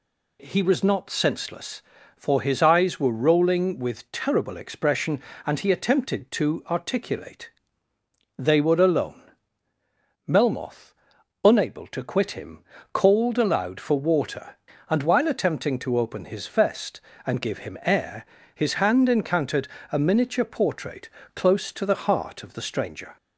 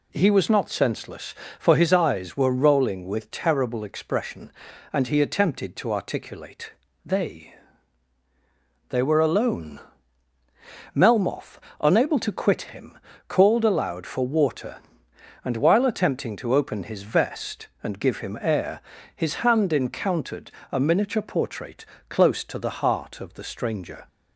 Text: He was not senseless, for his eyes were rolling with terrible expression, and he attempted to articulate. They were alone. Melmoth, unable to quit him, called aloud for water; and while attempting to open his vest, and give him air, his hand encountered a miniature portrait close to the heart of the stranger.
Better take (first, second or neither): first